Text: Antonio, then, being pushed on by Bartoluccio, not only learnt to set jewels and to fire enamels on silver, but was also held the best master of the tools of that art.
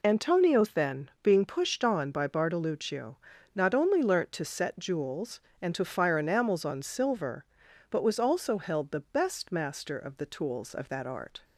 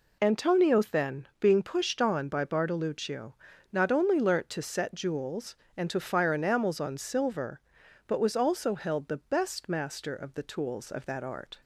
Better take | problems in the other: neither | none

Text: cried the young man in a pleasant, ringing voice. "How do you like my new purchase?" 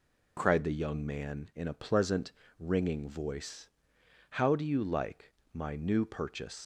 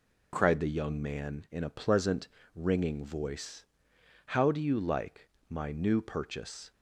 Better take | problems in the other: second | pauses between "like" and "my"; slight; at 5.3 s; 0.20 s long; slight in the second // leaves "purchase" unfinished; at 6.6 s; 110 ms

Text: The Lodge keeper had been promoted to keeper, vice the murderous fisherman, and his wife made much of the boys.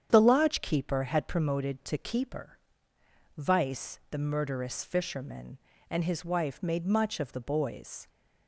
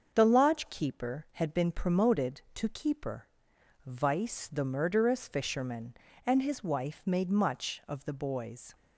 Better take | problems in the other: second | starts louder than the rest; strong; until 1.1 s; 8.5 dB; also in the second // skips "been"; at 1.2 s

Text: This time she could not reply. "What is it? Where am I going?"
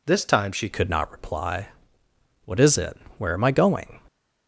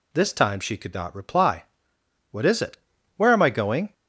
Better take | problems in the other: second | changes voice at "could"; from 0.7 s on; 3.2 s long

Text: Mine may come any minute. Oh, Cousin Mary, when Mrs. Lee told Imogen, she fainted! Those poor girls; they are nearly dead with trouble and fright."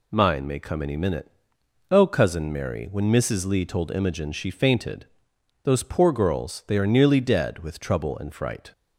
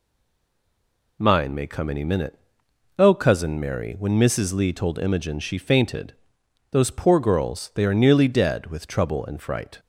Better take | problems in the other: first | stays silent before the first word; noticeable; until 1.1 s; 1.1 s long

